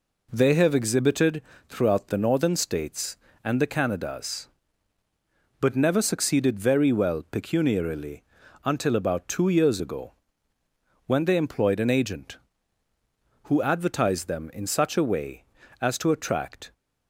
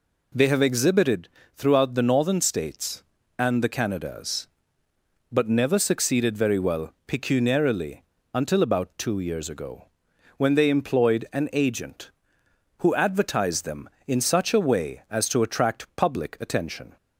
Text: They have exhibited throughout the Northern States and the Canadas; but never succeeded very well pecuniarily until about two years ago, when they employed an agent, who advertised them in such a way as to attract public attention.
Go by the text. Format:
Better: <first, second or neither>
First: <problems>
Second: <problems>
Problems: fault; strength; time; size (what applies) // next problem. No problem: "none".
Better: second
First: pauses between "exhibited" and "throughout"; slight; at 1.4 s; 0.26 s long // pauses between "pecuniarily" and "until"; at 8.2 s; 0.42 s long // stops before "public attention"; at 16.7 s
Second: pauses between "exhibited" and "throughout"; slight; at 1.2 s; 0.24 s long // pauses between "pecuniarily" and "until"; slight; at 8.0 s; 0.32 s long